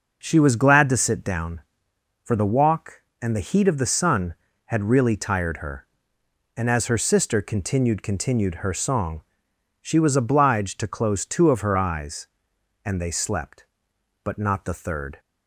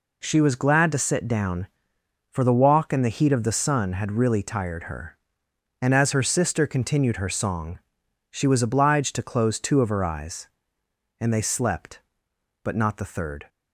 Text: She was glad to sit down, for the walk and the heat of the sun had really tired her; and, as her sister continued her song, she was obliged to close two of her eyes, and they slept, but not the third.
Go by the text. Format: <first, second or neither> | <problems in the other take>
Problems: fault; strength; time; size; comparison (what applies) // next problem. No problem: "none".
second | says "continued" twice; at 8.0 s